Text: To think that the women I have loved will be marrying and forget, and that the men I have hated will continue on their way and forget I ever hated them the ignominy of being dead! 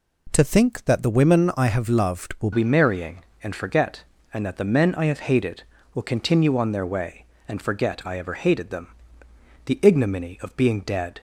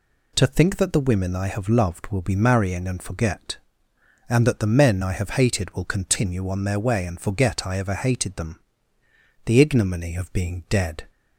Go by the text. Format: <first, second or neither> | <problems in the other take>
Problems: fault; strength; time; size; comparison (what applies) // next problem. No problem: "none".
second | changes voice at "be"; from 2.5 s on; 8.6 s long // pauses between "them" and "the"; noticeable; at 8.8 s; 0.78 s long; noticeable in the second